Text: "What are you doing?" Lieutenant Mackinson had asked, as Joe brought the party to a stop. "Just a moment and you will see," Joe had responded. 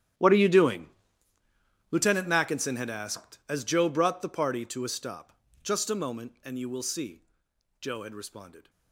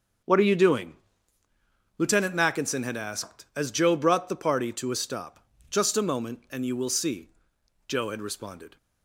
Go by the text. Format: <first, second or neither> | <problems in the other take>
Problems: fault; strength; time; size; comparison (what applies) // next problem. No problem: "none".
second | gets quieter; strong; throughout; 19.5 dB // starts louder than the rest; strong; until 2.2 s; 10.5 dB; also in the second